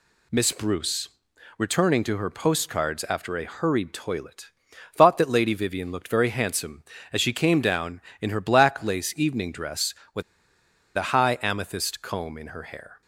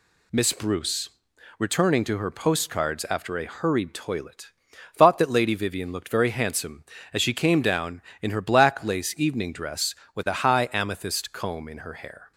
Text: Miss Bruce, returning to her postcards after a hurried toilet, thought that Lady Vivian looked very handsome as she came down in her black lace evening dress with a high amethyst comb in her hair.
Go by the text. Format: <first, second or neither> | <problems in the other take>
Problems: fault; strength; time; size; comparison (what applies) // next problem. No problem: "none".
second | pauses between "with" and "a"; noticeable; at 10.2 s; 0.74 s long